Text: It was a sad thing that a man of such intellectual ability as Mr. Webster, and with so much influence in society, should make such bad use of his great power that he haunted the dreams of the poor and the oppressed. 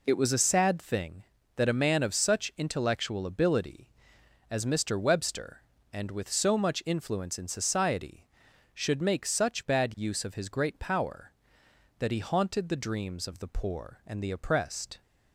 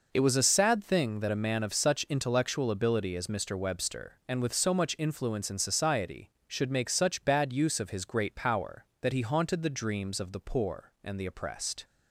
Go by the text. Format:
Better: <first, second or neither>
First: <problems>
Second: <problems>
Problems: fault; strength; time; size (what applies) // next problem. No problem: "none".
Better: neither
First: none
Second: none